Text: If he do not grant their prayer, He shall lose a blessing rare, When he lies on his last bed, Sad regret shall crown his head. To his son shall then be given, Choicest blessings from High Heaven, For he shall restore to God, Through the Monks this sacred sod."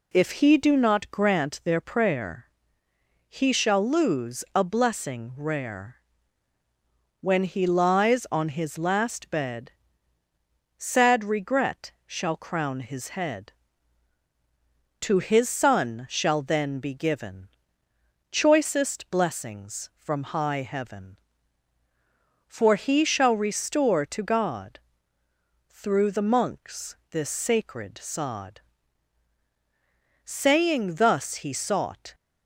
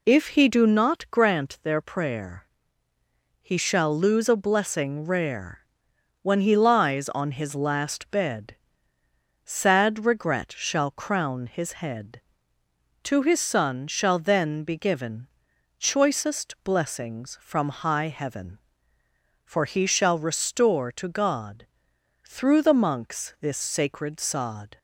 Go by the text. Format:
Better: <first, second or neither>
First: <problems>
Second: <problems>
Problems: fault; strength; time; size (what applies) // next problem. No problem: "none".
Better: second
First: pauses between "Monks" and "this"; slight; at 26.9 s; 0.16 s long // goes on to say "Saying thus he sought"; strong; from 30.2 s on; 1.9 s long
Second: none